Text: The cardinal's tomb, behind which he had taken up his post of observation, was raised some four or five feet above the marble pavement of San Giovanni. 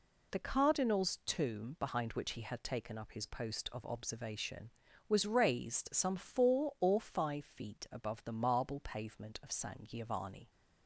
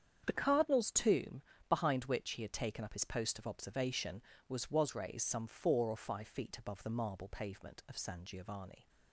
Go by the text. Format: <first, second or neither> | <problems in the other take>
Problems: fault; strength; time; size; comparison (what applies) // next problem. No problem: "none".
first | starts louder than the rest; strong; until 1.2 s; 8 dB // says "was" twice; at 4.7 s